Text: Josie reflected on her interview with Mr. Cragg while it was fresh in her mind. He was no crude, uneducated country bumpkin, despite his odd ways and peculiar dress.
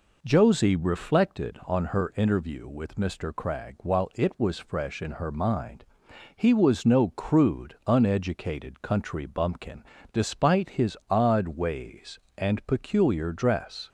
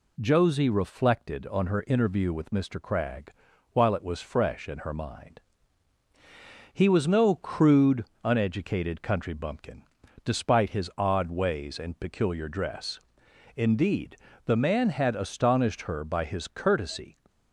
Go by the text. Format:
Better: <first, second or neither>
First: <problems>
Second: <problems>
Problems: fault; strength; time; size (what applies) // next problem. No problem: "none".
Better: first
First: none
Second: pauses between "Cragg" and "while"; at 3.3 s; 0.42 s long // goes on to say "Indeed the man had astonished her by his courtesy"; strong; from 13.5 s on; 3.6 s long